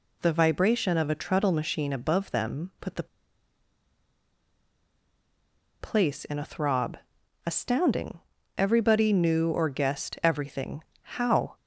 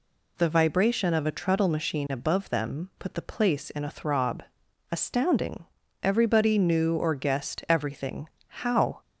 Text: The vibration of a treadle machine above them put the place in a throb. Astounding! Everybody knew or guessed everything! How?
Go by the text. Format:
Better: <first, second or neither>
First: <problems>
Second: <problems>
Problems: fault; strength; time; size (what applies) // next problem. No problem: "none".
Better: second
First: pauses between "the" and "place"; strong; at 3.0 s; 2.7 s long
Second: none